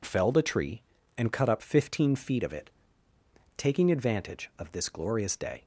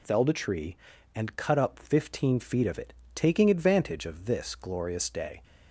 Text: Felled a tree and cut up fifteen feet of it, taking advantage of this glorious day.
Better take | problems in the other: neither | none

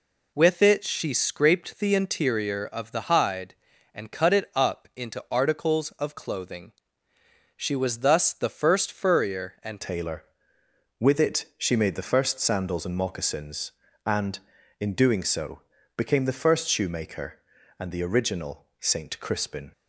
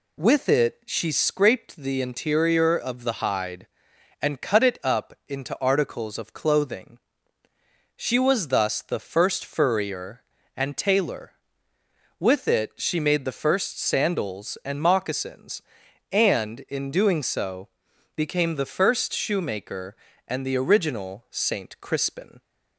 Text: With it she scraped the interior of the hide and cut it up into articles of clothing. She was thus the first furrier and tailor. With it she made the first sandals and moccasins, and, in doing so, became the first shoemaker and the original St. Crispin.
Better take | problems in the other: second | changes voice at "tailor"; from 9.8 s on; 9.9 s long

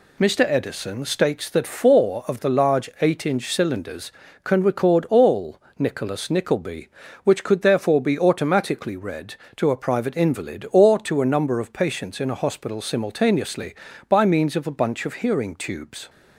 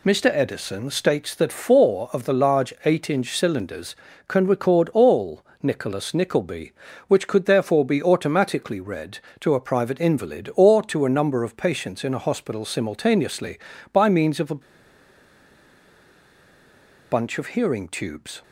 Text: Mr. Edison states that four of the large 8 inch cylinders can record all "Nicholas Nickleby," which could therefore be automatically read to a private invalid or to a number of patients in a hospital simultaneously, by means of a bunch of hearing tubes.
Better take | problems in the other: first | pauses between "all" and "Nicholas"; slight; at 5.4 s; 0.16 s long; slight in the first // pauses between "a" and "bunch"; strong; at 14.5 s; 2.5 s long

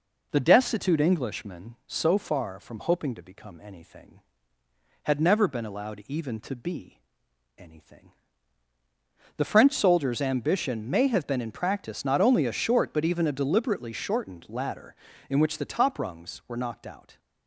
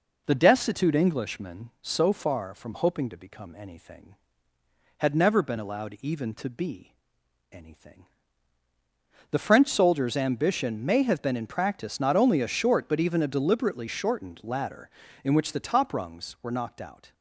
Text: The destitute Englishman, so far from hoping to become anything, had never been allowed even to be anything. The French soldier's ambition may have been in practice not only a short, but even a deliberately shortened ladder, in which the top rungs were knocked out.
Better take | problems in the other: neither | pauses between "be" and "anything"; noticeable; the same in both

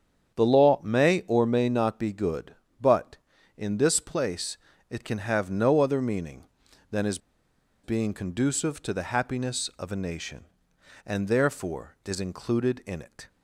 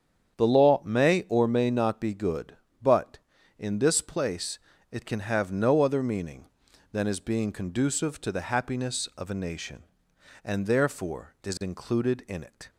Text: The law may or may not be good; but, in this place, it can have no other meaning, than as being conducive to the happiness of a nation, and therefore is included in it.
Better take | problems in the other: second | starts louder than the rest; strong; until 1.4 s; 8 dB; strong in the second // pauses between "as" and "being"; noticeable; at 7.1 s; 0.64 s long

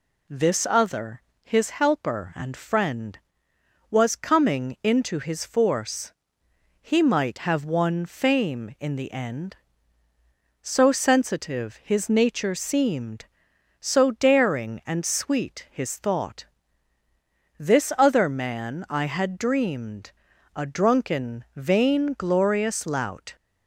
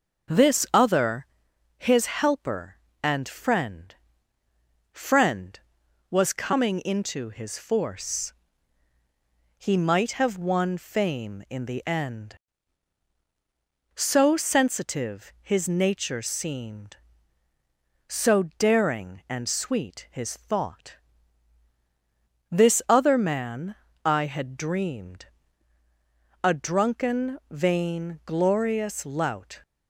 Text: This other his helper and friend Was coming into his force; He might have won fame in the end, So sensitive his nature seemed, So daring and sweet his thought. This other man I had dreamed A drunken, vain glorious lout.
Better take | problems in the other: first | pauses between "other" and "his"; noticeable; at 1.2 s; 0.54 s long; slight in the first // says "friend" twice; at 4.9 s // pauses between "So" and "daring"; slight; at 18.4 s; 0.16 s long // pauses between "man" and "I"; slight; at 23.7 s; 0.32 s long // pauses between "dreamed" and "A"; at 25.2 s; 1.1 s long; also in the first

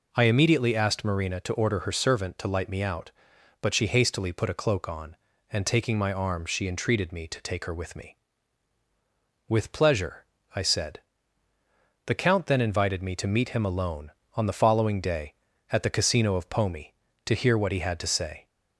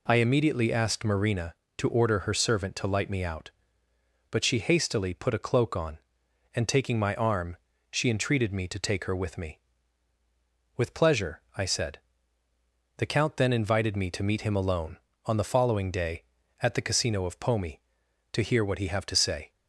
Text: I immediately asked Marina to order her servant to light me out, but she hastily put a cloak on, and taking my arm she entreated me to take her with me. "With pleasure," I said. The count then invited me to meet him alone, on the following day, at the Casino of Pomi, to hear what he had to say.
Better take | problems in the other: first | pauses between "arm" and "she"; slight; at 7.5 s; 0.34 s long // says "have" for "had"; at 18.8 s

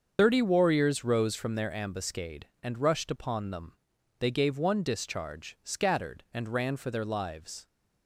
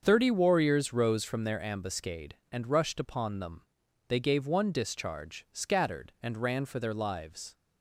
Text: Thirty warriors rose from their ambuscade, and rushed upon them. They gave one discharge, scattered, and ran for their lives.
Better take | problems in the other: second | loses the start of "Thirty"; at 0.1 s; 50 ms // starts louder than the rest; until 1.1 s; 6.5 dB; also in the second

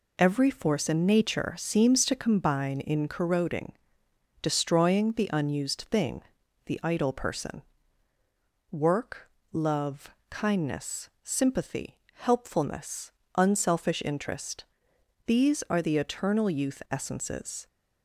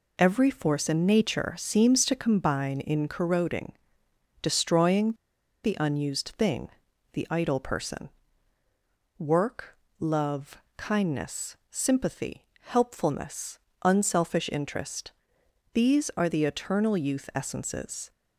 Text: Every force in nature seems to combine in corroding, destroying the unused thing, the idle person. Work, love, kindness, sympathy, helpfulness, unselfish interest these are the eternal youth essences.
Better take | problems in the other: first | pauses between "destroying" and "the"; noticeable; at 5.1 s; 0.50 s long // pauses between "interest" and "these"; noticeable; at 15.1 s; 0.60 s long; noticeable in the first

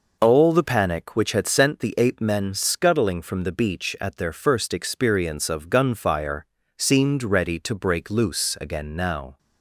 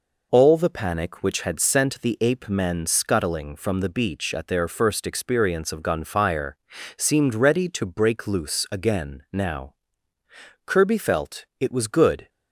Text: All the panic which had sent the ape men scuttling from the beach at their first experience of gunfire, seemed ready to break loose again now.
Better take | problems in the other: first | goes on to say "Kirby felt it was good"; from 10.6 s on; 1.6 s long

